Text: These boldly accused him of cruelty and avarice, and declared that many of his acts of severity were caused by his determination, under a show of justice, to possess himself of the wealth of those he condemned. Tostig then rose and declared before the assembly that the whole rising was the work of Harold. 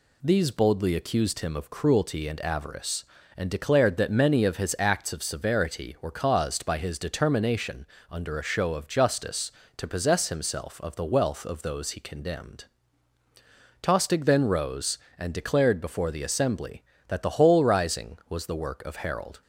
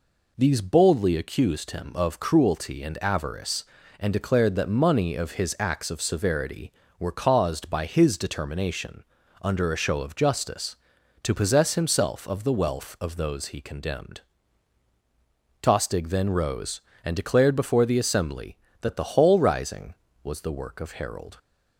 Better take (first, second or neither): first